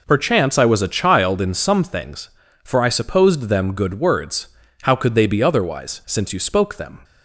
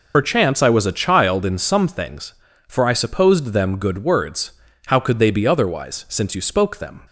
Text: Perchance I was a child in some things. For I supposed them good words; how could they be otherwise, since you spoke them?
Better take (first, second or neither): first